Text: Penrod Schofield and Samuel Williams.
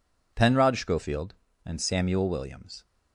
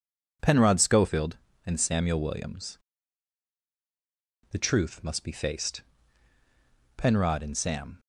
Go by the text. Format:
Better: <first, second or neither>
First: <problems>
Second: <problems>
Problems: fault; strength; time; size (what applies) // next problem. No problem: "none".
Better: first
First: none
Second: goes on to say "The truth must be faced Penrod and Sam"; strong; from 4.5 s on; 3.4 s long